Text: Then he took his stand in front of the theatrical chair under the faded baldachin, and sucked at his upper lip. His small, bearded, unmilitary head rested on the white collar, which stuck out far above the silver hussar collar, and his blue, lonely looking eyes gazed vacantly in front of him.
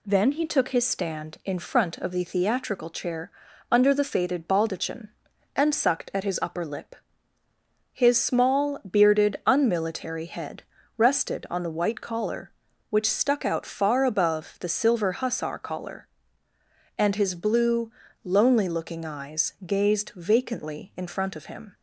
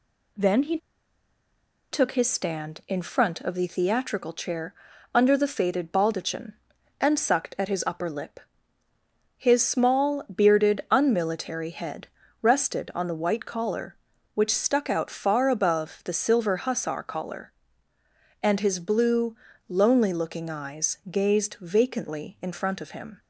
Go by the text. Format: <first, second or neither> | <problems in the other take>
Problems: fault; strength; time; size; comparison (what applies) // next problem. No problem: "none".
first | pauses between "he" and "took"; at 0.7 s; 1.1 s long // pauses between "chair" and "under"; at 4.7 s; 0.40 s long; also in the first // pauses between "head" and "rested"; slight; at 12.0 s; 0.34 s long; slight in the first